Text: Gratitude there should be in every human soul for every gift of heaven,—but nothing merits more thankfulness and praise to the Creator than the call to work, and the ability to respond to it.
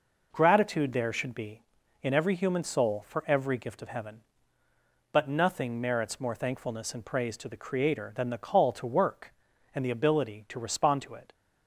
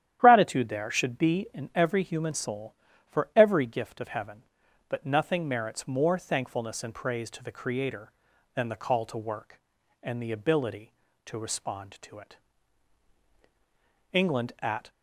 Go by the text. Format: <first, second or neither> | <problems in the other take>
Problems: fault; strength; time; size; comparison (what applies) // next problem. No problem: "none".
first | starts louder than the rest; strong; until 1.2 s; 10.5 dB // goes on to say "England at"; noticeable; from 14.1 s on; 0.78 s long